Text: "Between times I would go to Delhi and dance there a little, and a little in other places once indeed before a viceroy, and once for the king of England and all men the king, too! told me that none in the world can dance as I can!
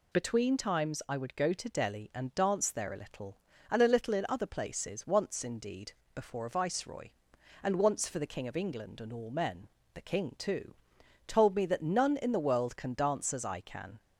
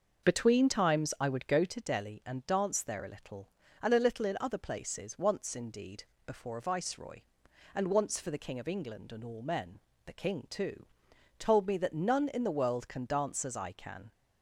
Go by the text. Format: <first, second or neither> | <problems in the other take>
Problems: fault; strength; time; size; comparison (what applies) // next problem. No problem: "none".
first | starts louder than the rest; until 1.8 s; 6 dB // pauses between "indeed" and "before"; slight; at 6.0 s; 0.20 s long; slight in the first // pauses between "men" and "the"; slight; at 9.8 s; 0.24 s long; slight in the first